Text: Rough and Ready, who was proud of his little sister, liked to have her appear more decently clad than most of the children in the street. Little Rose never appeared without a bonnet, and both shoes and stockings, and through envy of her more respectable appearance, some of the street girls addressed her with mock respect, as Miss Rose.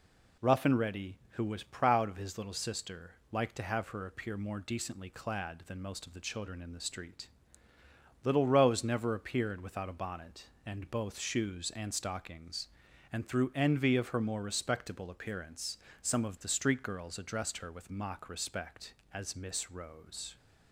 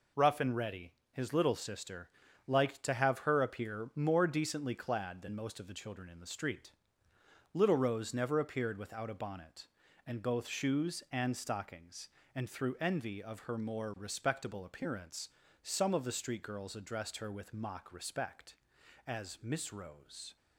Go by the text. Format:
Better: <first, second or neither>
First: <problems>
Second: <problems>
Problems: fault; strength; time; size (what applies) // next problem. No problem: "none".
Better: first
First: none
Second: skips "who was proud of"; at 1.0 s